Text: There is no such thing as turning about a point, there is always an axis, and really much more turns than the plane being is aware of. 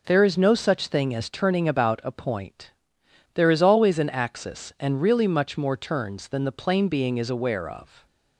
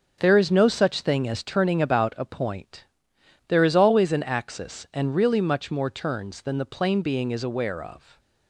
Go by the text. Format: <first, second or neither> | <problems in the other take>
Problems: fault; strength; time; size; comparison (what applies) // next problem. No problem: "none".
first | gets quieter; strong; throughout; 9 dB